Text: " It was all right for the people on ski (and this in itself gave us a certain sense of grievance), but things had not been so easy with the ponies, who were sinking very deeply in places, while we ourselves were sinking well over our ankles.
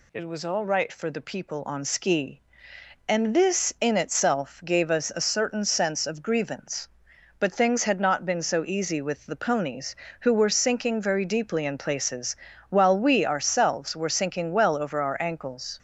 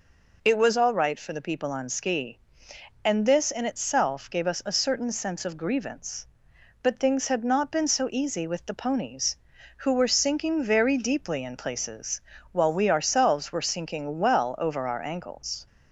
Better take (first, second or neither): neither